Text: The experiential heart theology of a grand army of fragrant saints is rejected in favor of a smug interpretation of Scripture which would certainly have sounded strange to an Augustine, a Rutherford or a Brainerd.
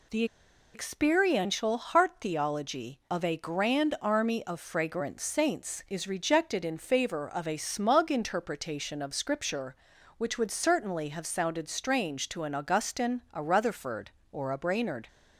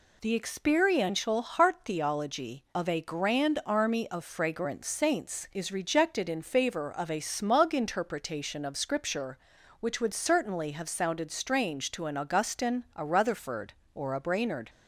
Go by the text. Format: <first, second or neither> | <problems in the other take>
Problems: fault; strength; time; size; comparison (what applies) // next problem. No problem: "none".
second | pauses between "The" and "experiential"; noticeable; at 0.2 s; 0.49 s long